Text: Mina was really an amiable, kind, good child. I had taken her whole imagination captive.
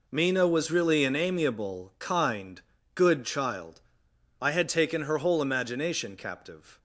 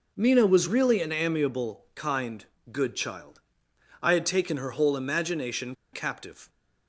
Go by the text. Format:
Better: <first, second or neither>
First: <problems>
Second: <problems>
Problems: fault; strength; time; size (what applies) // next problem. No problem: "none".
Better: first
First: none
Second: pauses between "imagination" and "captive"; slight; at 5.7 s; 0.19 s long